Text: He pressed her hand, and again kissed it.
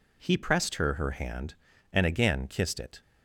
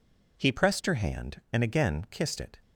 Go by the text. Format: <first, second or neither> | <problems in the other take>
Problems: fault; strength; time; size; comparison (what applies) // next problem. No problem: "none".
second | says "her" twice; at 0.9 s